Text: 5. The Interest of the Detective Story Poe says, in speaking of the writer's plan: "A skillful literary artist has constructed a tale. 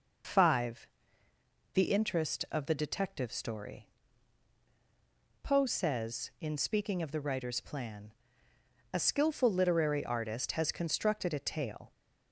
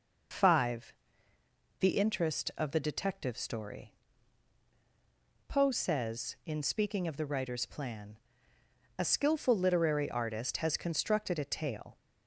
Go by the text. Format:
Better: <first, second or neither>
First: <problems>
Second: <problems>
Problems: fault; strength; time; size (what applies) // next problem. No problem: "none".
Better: neither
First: pauses between "Story" and "Poe"; strong; at 3.8 s; 1.5 s long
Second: pauses between "Story" and "Poe"; strong; at 3.9 s; 1.5 s long